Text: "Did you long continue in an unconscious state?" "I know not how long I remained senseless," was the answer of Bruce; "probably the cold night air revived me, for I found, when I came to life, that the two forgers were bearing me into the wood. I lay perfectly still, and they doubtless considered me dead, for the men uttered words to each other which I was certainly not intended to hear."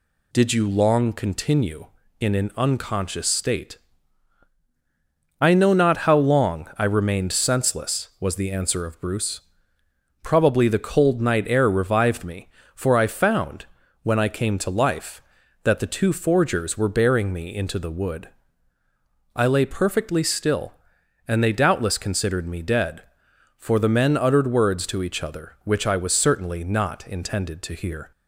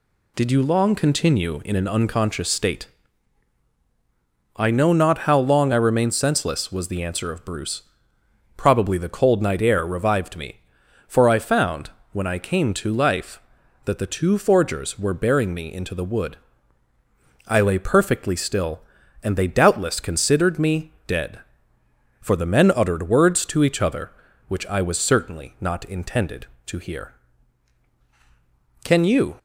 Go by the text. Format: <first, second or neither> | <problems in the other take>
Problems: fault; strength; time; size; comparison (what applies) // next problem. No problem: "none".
first | goes on to say "Can you"; from 28.8 s on; 0.54 s long